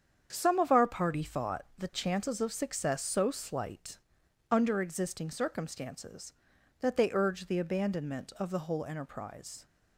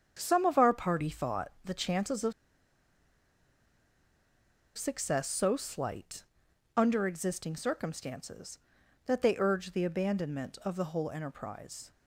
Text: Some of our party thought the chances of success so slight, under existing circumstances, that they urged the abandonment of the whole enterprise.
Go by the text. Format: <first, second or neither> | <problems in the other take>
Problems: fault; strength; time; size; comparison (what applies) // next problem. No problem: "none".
first | starts louder than the rest; strong; until 1.1 s; 7.5 dB; strong in the first // pauses between "of" and "success"; strong; at 2.3 s; 2.4 s long